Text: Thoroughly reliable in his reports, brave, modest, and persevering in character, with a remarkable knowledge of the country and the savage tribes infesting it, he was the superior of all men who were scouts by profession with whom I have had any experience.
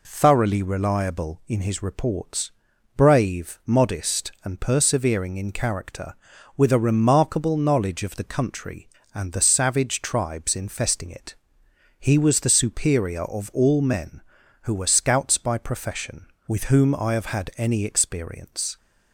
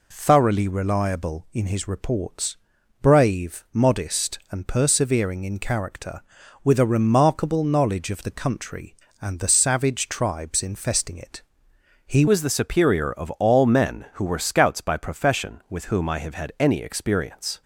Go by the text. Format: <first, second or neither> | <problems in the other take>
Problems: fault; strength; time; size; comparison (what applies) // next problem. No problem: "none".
first | changes voice at "was"; from 12.2 s on; 5.4 s long